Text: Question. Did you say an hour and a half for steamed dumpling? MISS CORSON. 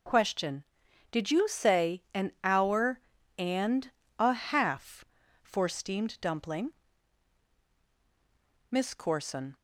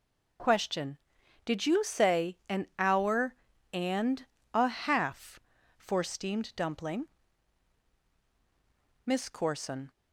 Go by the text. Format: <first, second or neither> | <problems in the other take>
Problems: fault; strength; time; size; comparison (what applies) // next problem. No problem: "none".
neither | pauses between "and" and "a"; slight; the same in both